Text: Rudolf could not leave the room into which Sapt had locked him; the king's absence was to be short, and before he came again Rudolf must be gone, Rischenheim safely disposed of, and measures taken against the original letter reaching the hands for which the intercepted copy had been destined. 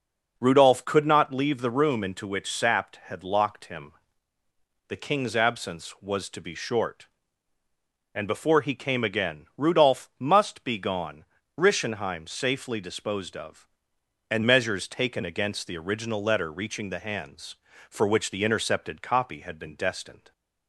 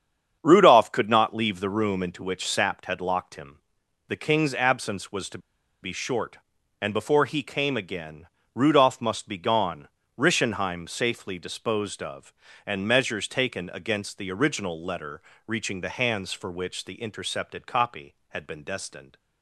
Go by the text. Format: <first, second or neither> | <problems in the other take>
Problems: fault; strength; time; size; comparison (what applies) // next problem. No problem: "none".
first | starts louder than the rest; strong; until 1.4 s; 8 dB // pauses between "to" and "be"; at 5.3 s; 0.44 s long // pauses between "again" and "Rudolf"; slight; at 8.2 s; 0.26 s long // pauses between "letter" and "reaching"; slight; at 15.2 s; 0.26 s long